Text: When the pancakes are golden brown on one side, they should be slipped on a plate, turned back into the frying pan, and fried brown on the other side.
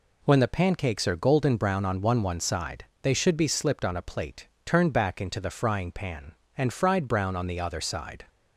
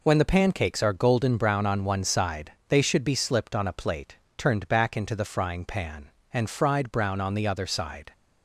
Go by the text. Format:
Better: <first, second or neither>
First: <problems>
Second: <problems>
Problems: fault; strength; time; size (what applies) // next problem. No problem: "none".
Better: second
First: says "one" twice; at 2.2 s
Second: none